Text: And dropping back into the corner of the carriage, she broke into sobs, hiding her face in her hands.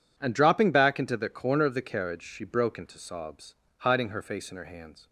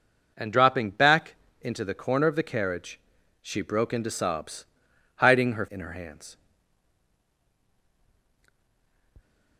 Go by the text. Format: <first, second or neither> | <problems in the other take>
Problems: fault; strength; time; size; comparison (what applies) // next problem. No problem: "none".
first | pauses between "back" and "into"; slight; at 1.3 s; 0.24 s long // skips "face"; at 5.6 s